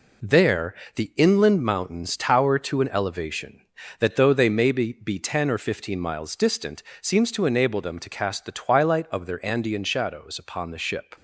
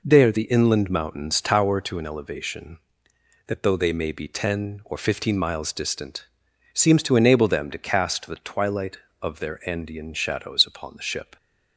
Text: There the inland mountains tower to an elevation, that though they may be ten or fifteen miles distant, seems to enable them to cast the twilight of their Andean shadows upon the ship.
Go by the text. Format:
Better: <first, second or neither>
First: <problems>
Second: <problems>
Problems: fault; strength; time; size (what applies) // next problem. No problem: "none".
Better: second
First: pauses between "There" and "the"; slight; at 0.7 s; 0.20 s long // says "be" twice; at 4.9 s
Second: none